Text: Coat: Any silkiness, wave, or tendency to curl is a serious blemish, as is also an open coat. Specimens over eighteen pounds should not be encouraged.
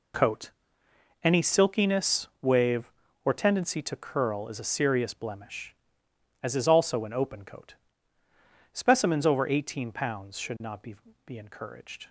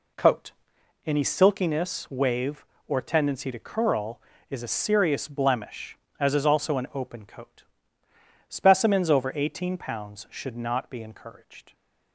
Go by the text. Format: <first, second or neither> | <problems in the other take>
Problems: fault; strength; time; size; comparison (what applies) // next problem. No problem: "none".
second | says "be" twice; at 11.2 s